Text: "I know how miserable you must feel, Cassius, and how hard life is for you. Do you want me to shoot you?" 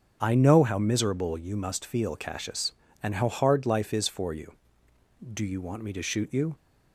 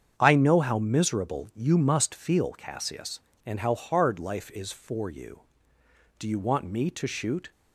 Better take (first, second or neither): first